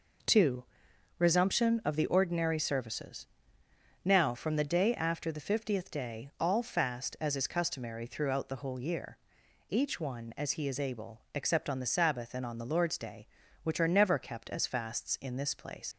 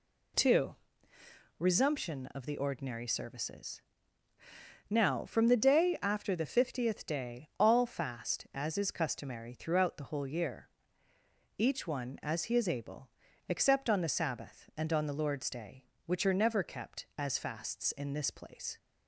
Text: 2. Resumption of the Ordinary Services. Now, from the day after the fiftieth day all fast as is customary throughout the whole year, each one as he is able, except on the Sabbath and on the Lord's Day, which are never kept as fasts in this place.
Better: second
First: leaves "place" unfinished; at 15.9 s; 75 ms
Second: none

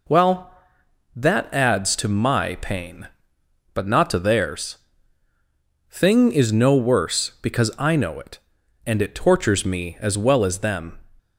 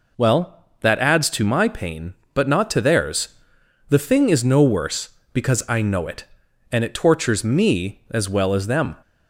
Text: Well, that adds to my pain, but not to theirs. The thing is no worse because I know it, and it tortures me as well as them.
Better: second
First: skips "The"; at 5.3 s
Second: none

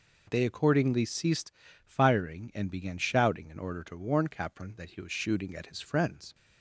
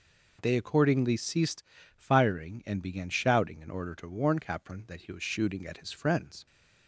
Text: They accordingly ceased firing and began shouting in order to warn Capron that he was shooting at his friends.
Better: neither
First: pauses between "ceased" and "firing"; slight; at 1.5 s; 0.34 s long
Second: pauses between "ceased" and "firing"; slight; at 1.6 s; 0.34 s long

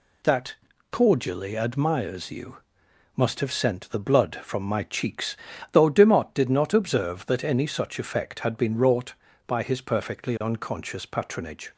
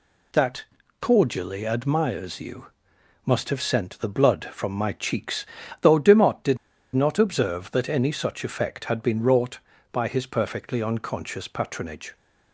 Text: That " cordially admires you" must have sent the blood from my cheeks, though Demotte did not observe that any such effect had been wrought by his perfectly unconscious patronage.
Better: first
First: pauses between "you" and "must"; noticeable; at 2.5 s; 0.58 s long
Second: pauses between "you" and "must"; noticeable; at 2.6 s; 0.58 s long // pauses between "did" and "not"; at 6.5 s; 0.37 s long

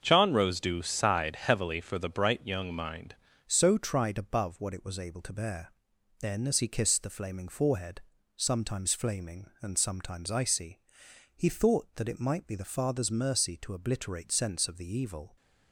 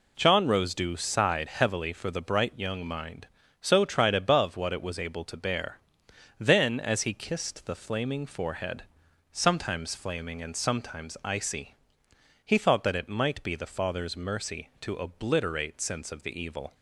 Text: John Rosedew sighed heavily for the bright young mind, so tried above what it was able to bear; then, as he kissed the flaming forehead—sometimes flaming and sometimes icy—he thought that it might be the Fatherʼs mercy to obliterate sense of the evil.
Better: second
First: starts louder than the rest; until 1.0 s; 7 dB // changes voice at "so"; from 3.4 s on; 11.9 s long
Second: none

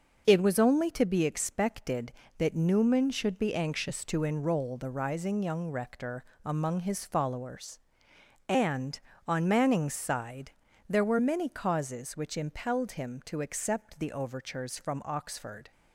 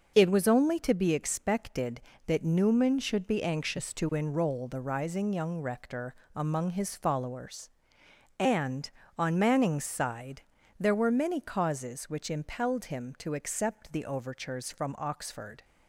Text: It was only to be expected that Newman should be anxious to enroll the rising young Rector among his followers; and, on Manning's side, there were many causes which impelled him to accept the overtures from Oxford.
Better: neither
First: pauses between "Rector" and "among"; slight; at 6.2 s; 0.20 s long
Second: pauses between "Rector" and "among"; slight; at 6.1 s; 0.20 s long

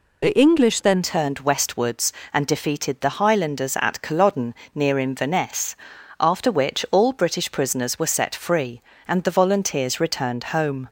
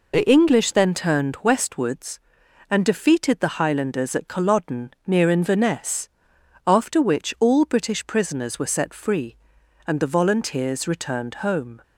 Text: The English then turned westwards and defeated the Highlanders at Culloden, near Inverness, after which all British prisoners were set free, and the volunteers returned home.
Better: second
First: changes voice at "turned"; from 1.0 s on; 9.8 s long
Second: none

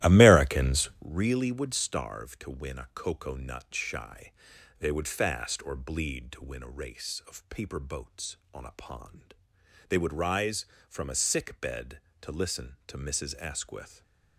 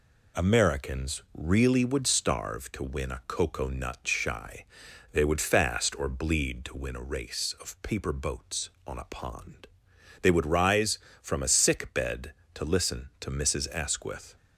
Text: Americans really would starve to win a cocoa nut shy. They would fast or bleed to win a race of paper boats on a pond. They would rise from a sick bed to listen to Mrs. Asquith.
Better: second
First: starts louder than the rest; strong; until 1.1 s; 14.5 dB // stays silent after the last word; slight; from 13.8 s on; 0.5 s long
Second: none

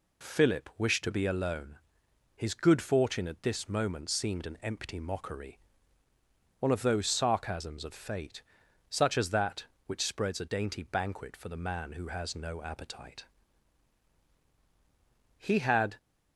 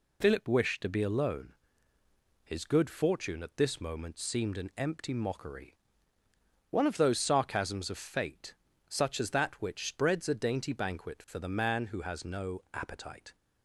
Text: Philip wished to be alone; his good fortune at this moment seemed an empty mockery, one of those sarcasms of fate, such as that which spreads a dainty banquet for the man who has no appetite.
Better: second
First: goes on to say "He had"; from 15.3 s on; 0.60 s long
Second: none

